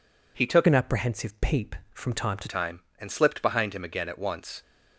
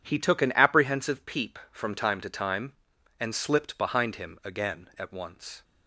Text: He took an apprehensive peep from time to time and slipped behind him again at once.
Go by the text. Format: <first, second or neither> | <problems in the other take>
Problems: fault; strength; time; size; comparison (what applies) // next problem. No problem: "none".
second | changes voice from "an" to "to"; from 0.6 to 2.4 s; 1.8 s long